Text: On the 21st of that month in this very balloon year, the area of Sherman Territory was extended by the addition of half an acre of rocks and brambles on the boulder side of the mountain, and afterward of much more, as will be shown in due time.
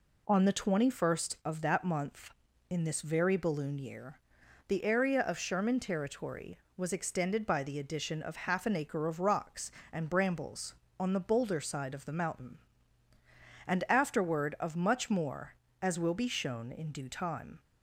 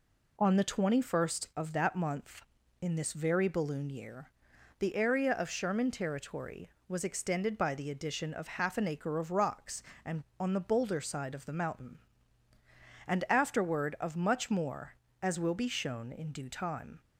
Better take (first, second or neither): first